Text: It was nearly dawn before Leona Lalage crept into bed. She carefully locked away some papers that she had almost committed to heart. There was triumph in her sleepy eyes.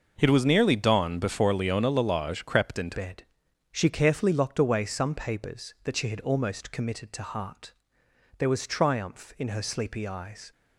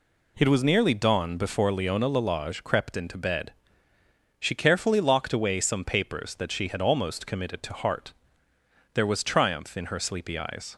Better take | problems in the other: second | changes voice at "bed"; from 2.9 s on; 7.6 s long

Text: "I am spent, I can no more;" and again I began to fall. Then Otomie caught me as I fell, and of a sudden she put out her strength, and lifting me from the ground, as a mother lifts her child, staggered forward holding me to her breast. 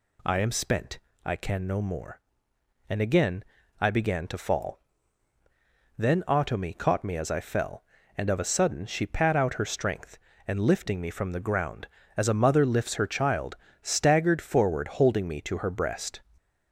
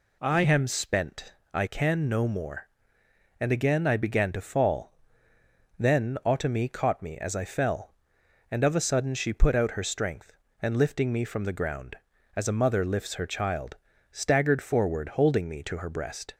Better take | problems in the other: second | pauses between "again" and "I"; at 3.4 s; 0.38 s long // says "pat" for "put"; at 9.0 s

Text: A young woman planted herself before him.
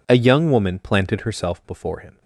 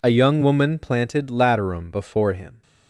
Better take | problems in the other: first | says "laterum" for "herself"; at 1.2 s

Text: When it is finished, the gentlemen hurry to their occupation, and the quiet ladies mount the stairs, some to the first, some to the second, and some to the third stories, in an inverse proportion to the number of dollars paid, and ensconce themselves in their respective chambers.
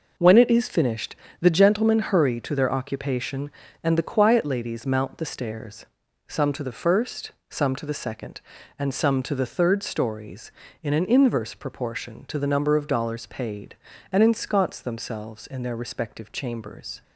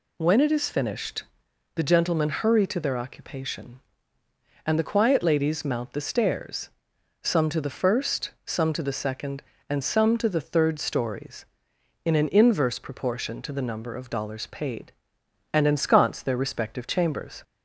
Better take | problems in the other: first | skips "themselves in"; at 16.2 s

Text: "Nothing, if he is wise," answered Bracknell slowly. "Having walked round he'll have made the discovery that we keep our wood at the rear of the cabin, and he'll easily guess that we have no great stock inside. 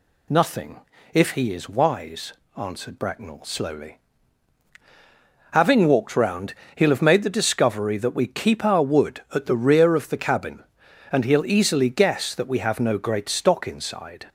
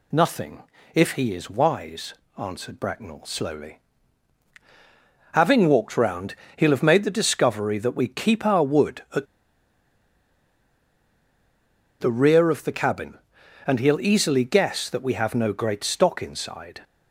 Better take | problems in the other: first | pauses between "round" and "he'll"; slight; at 6.3 s; 0.18 s long; slight in the first // pauses between "at" and "the"; strong; at 9.2 s; 2.7 s long

